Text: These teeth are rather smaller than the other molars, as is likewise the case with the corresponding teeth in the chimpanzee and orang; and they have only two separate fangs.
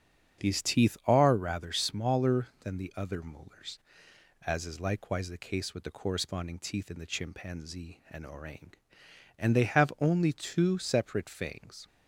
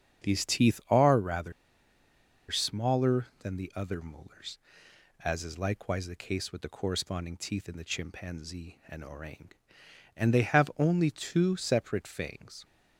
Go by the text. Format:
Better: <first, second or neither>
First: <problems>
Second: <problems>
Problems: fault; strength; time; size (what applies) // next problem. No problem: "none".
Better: first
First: starts louder than the rest; strong; until 1.5 s; 7.5 dB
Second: starts louder than the rest; strong; until 1.3 s; 7.5 dB // pauses between "rather" and "smaller"; at 1.5 s; 0.99 s long